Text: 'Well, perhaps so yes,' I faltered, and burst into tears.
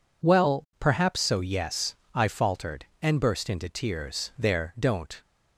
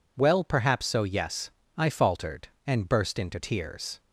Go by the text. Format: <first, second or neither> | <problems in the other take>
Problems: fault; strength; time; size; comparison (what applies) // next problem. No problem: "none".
second | goes on to say "There don't"; noticeable; from 4.3 s on; 0.84 s long